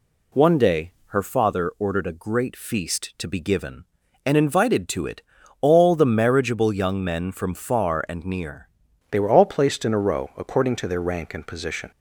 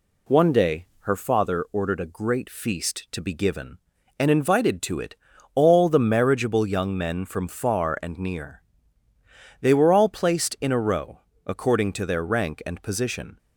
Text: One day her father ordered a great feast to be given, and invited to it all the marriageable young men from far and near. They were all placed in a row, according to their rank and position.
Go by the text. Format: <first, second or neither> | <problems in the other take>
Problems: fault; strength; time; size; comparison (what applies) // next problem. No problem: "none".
second | pauses between "it" and "all"; at 5.2 s; 0.38 s long; also in the second // changes voice at "They"; from 9.1 s on; 2.8 s long